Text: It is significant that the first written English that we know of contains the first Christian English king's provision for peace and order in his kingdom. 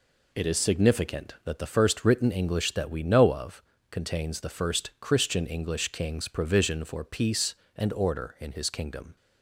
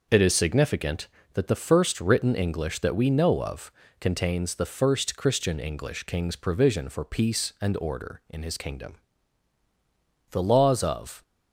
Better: first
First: pauses between "of" and "contains"; slight; at 3.6 s; 0.28 s long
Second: pauses between "of" and "contains"; slight; at 3.7 s; 0.30 s long // goes on to say "The laws of"; noticeable; from 10.3 s on; 0.92 s long

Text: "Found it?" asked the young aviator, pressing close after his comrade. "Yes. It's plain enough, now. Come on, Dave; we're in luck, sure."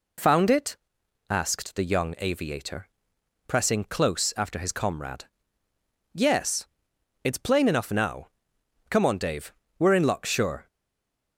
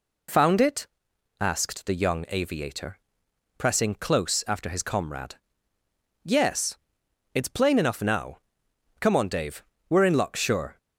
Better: second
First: stays silent after the last word; slight; from 10.6 s on; 0.7 s long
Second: none

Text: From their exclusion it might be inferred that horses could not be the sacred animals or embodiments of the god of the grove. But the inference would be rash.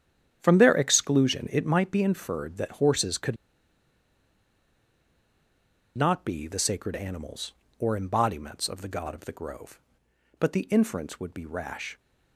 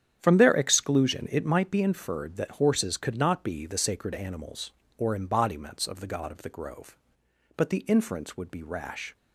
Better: second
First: starts louder than the rest; strong; until 1.4 s; 9 dB // pauses between "could" and "not"; strong; at 3.3 s; 2.6 s long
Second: starts louder than the rest; strong; until 1.2 s; 9 dB

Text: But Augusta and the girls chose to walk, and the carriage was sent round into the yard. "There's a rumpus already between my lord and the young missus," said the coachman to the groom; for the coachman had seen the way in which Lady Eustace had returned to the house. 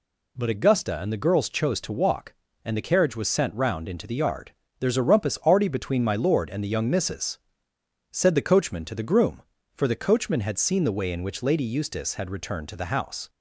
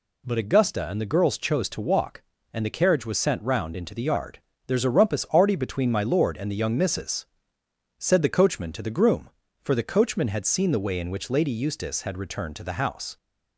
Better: neither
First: none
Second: none

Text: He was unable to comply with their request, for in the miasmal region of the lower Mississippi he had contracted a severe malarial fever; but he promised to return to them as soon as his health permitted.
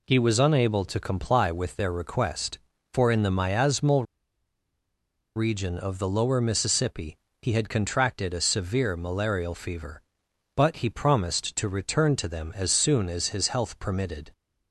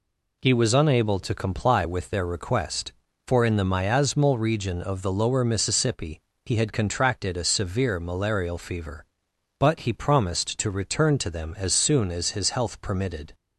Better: second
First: pauses between "miasmal" and "region"; strong; at 4.0 s; 1.3 s long // pauses between "Mississippi" and "he"; slight; at 7.1 s; 0.26 s long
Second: pauses between "Mississippi" and "he"; slight; at 6.1 s; 0.26 s long

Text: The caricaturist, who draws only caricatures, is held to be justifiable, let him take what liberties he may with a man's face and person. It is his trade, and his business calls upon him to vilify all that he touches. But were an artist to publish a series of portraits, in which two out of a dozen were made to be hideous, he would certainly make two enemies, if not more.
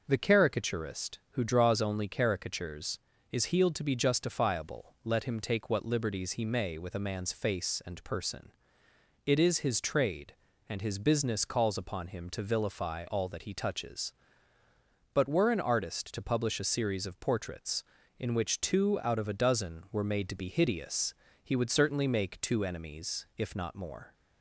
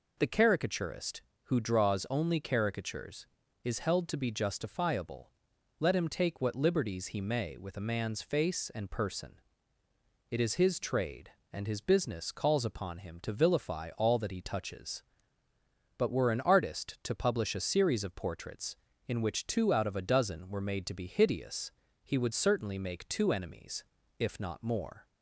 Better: second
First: says "healed" for "held"; at 3.4 s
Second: none

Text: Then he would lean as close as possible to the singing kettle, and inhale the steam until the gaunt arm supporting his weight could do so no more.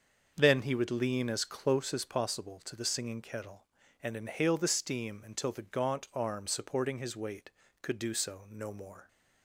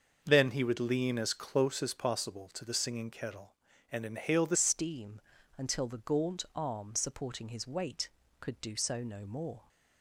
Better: first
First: starts louder than the rest; until 1.3 s; 6.5 dB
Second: starts louder than the rest; until 1.2 s; 6.5 dB // changes voice at "steam"; from 4.5 s on; 5.1 s long // pauses between "steam" and "until"; slight; at 5.2 s; 0.36 s long

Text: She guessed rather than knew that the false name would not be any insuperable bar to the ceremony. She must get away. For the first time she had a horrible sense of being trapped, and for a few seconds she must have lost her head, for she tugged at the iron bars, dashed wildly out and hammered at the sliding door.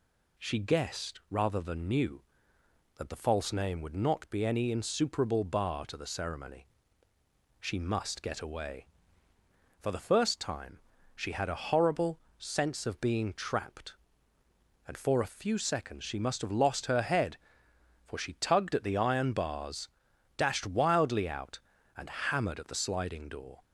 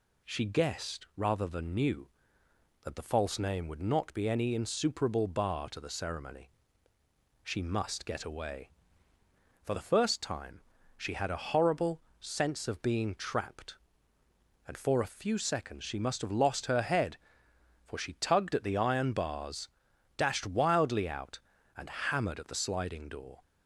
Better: neither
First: pauses between "time" and "she"; slight; at 10.7 s; 0.36 s long // pauses between "horrible" and "sense"; slight; at 12.1 s; 0.20 s long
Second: pauses between "time" and "she"; slight; at 10.6 s; 0.36 s long // pauses between "horrible" and "sense"; slight; at 12.0 s; 0.20 s long

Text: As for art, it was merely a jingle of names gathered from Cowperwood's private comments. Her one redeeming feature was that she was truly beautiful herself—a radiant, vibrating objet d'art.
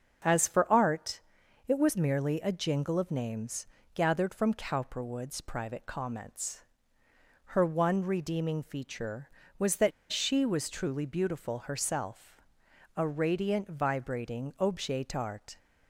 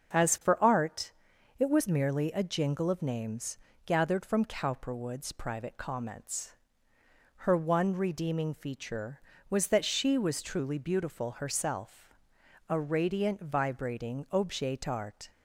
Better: second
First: starts louder than the rest; until 1.7 s; 6.5 dB // pauses between "names" and "gathered"; slight; at 3.6 s; 0.26 s long // pauses between "that" and "she"; slight; at 9.9 s; 0.20 s long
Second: starts louder than the rest; until 1.6 s; 7 dB // pauses between "names" and "gathered"; slight; at 3.5 s; 0.26 s long

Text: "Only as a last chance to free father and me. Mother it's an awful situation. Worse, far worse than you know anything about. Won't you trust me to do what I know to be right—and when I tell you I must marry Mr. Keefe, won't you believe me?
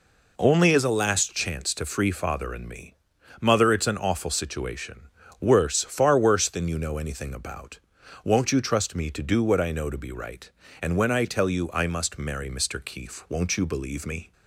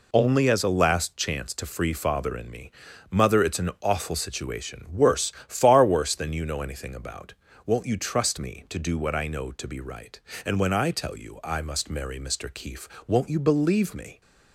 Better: neither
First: none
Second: none

